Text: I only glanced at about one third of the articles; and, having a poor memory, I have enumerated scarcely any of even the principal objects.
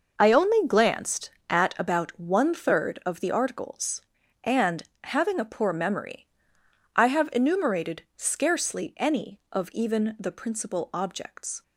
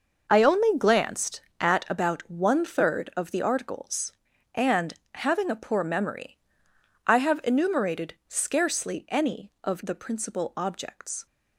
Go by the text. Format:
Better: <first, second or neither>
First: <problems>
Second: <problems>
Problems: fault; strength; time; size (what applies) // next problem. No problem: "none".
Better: first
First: none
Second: skips "even"; at 9.8 s